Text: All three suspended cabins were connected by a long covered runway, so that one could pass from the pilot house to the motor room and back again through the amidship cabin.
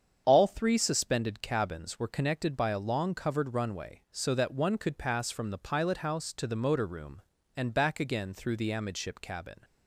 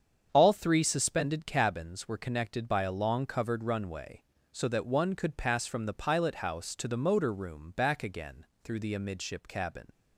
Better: first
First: starts louder than the rest; strong; until 1.2 s; 7.5 dB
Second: starts louder than the rest; strong; until 1.3 s; 7.5 dB // skips "and"; at 7.7 s // pauses between "again" and "through"; slight; at 8.4 s; 0.18 s long

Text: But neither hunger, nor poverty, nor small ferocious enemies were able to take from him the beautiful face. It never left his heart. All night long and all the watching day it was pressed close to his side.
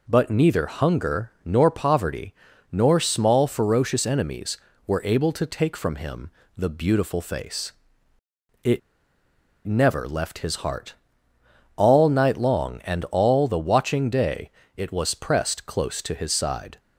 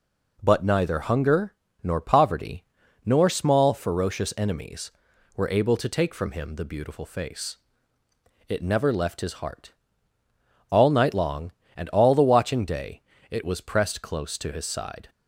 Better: second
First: pauses between "him" and "the"; slight; at 6.2 s; 0.28 s long // pauses between "It" and "never"; noticeable; at 8.7 s; 0.87 s long // pauses between "day" and "it"; slight; at 14.5 s; 0.24 s long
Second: pauses between "day" and "it"; slight; at 13.0 s; 0.30 s long

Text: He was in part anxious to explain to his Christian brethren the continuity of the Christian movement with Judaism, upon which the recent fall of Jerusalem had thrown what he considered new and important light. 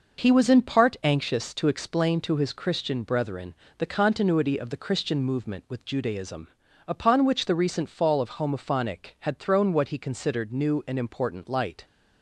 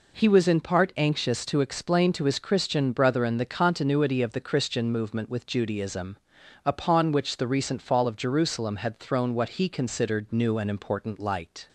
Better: second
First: pauses between "brethren" and "the"; slight; at 3.5 s; 0.22 s long // says "Homophonic" for "Jerusalem"; at 8.3 s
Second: none

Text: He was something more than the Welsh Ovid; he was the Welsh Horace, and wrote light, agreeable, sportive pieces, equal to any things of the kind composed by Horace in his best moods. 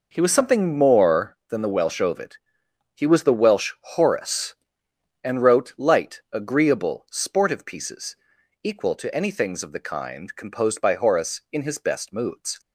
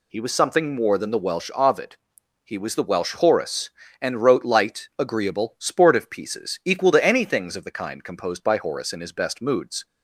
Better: neither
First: none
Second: none

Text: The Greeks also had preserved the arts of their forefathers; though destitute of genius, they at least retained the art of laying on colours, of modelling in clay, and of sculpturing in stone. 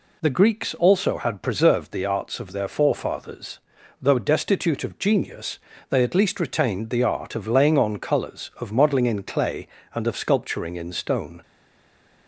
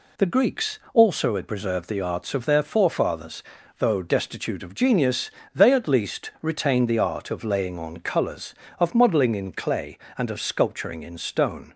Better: second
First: stays silent after the last word; slight; from 11.4 s on; 0.8 s long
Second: none

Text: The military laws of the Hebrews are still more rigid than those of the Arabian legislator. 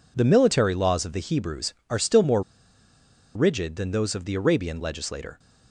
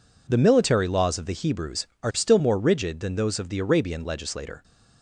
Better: second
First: pauses between "more" and "rigid"; noticeable; at 2.4 s; 0.93 s long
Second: none

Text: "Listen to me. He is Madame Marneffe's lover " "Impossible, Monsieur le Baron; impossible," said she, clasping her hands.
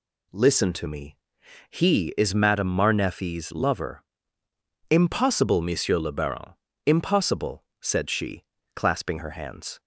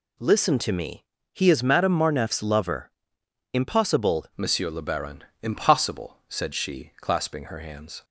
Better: first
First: none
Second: changes voice at "Monsieur"; from 4.3 s on; 3.7 s long

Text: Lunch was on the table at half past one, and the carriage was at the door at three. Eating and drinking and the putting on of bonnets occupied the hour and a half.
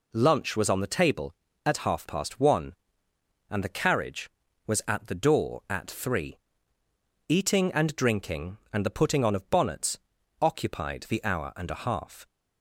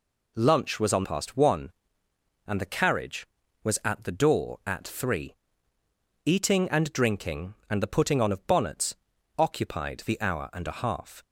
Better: first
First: pauses between "bonnets" and "occupied"; at 9.9 s; 0.42 s long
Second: skips "the table at half"; at 1.0 s // pauses between "bonnets" and "occupied"; at 8.9 s; 0.42 s long

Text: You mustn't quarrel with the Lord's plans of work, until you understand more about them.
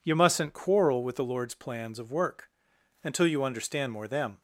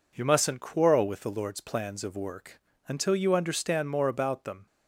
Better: second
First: skips "about"; at 4.0 s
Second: none

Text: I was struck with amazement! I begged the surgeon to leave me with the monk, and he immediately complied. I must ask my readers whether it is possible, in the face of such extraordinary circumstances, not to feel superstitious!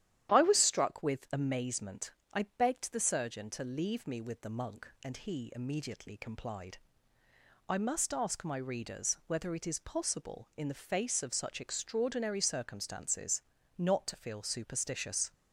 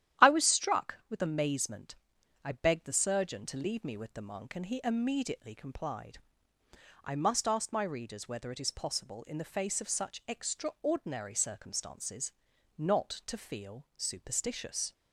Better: neither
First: starts louder than the rest; strong; until 1.3 s; 11 dB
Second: starts louder than the rest; strong; until 1.3 s; 11.5 dB

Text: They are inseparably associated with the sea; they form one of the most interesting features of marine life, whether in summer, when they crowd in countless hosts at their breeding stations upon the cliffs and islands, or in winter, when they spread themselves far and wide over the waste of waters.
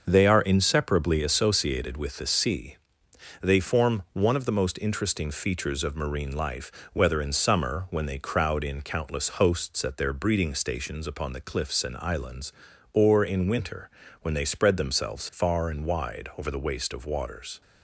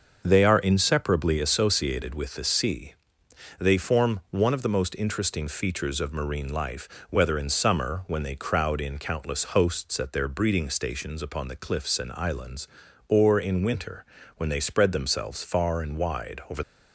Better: first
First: starts louder than the rest; noticeable; until 1.0 s; 6 dB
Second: starts louder than the rest; noticeable; until 1.2 s; 6 dB // stops before "the waste of waters"; at 16.6 s

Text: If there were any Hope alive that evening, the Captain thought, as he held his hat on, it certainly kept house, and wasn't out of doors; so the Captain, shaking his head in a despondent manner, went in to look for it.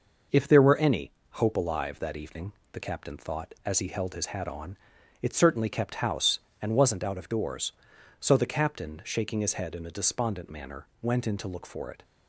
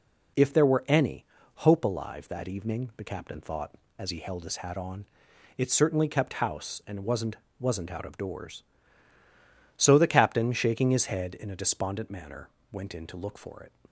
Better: first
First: pauses between "any" and "Hope"; slight; at 1.1 s; 0.24 s long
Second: pauses between "any" and "Hope"; slight; at 1.2 s; 0.34 s long // says "wasn't" twice; at 7.5 s

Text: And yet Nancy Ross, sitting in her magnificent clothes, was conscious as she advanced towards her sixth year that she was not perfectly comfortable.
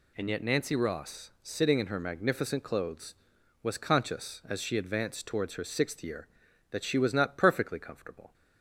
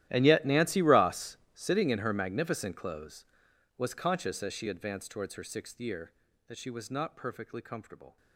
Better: first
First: none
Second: gets quieter; strong; throughout; 20.5 dB

